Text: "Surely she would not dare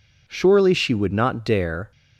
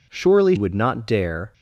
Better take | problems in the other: first | skips "she"; at 0.5 s

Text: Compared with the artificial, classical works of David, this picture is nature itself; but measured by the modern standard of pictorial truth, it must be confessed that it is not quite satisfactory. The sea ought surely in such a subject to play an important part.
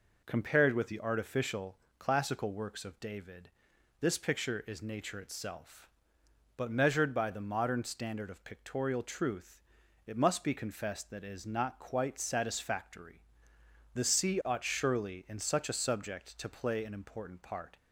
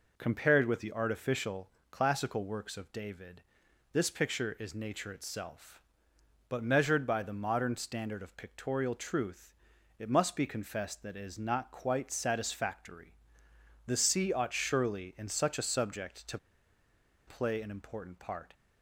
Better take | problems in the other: first | pauses between "to" and "play"; noticeable; at 16.3 s; 0.89 s long

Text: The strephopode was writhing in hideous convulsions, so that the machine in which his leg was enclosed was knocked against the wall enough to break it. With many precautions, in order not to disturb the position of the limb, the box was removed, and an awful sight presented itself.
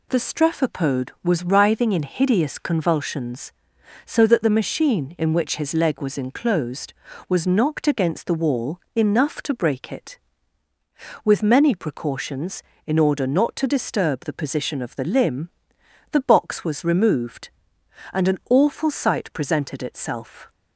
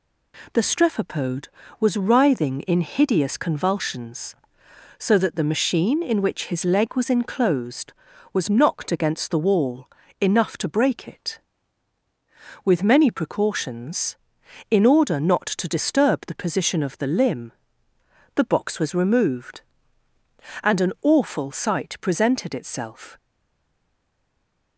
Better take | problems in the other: first | pauses between "wall" and "enough"; slight; at 9.8 s; 0.34 s long; slight in the first // stays silent after the last word; noticeable; from 23.1 s on; 1.6 s long

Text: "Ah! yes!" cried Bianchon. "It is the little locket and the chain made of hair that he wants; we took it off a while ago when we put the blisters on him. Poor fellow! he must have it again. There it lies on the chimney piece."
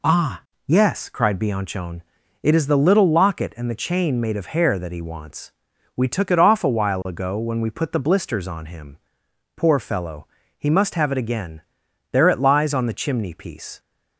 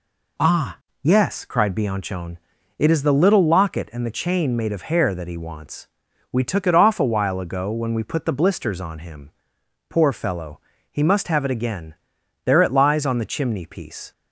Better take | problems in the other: neither | none

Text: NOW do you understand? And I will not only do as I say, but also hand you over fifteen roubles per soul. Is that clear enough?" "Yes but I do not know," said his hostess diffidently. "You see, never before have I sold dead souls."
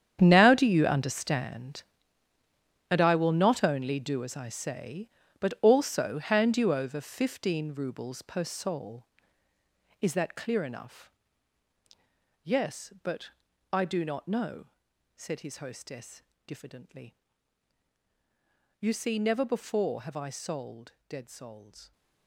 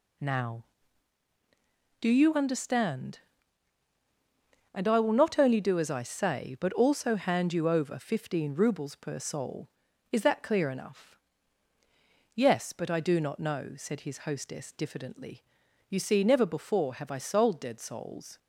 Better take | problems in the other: second | gets quieter; strong; throughout; 14 dB // pauses between "but" and "I"; at 13.2 s; 0.42 s long // pauses between "hostess" and "diffidently"; slight; at 16.2 s; 0.24 s long // pauses between "sold" and "dead"; slight; at 20.9 s; 0.16 s long

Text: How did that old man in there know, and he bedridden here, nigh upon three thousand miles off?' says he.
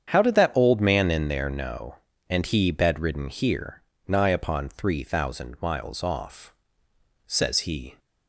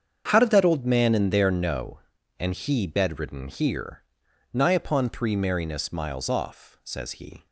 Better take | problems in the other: first | starts louder than the rest; strong; until 1.3 s; 7.5 dB; strong in the first // says "merriness" for "thousand"; at 5.3 s

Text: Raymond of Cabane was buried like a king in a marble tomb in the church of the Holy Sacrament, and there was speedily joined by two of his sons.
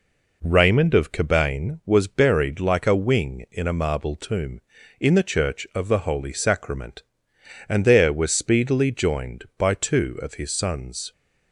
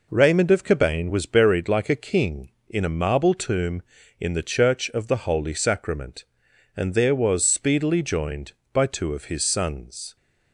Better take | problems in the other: second | says "wing" for "king"; at 2.9 s

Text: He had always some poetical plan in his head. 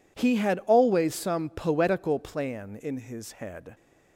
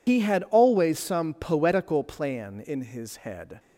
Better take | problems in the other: first | loses the start of "He"; at 0.0 s; 75 ms

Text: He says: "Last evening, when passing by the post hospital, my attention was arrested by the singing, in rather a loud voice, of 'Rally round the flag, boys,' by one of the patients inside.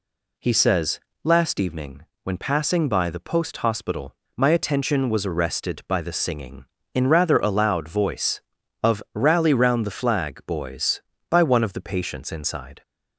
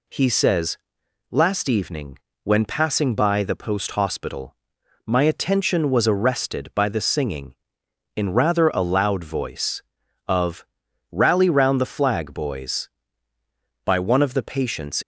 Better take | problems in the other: first | pauses between "of" and "Rally"; noticeable; at 10.6 s; 0.46 s long // stops before "inside"; at 15.0 s

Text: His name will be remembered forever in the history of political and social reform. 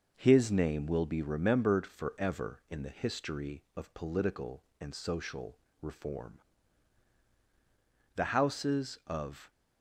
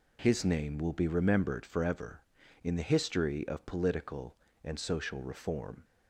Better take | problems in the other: second | pauses between "social" and "reform"; slight; at 5.5 s; 0.24 s long // goes on to say "The Houses of"; from 8.1 s on; 1.3 s long

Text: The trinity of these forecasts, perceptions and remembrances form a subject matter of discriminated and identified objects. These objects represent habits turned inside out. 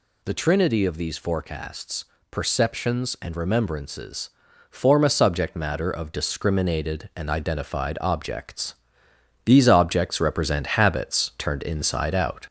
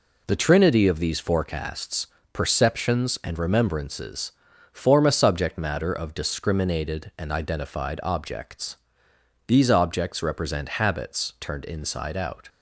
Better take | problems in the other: second | gets louder; throughout; 4 dB // pauses between "remembrances" and "form"; at 4.3 s; 0.40 s long; also in the second

